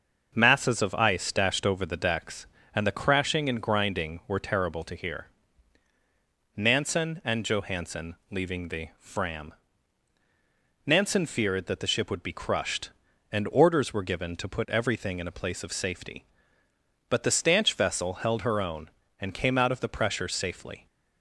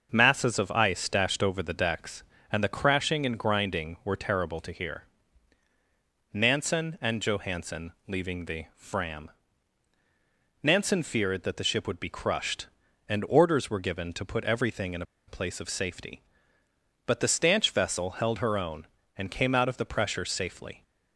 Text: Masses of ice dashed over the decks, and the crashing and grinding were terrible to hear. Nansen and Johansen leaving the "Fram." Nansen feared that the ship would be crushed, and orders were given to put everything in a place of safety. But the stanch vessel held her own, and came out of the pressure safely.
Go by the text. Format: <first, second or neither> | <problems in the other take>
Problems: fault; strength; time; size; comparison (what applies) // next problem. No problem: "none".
first | starts louder than the rest; until 1.1 s; 6.5 dB; also in the first // pauses between "Johansen" and "leaving"; slight; at 7.9 s; 0.16 s long; slight in the first // pauses between "in" and "a"; slight; at 15.0 s; 0.25 s long